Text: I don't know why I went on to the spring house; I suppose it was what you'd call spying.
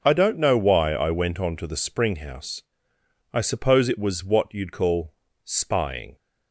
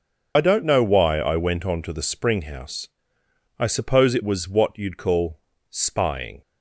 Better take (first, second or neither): first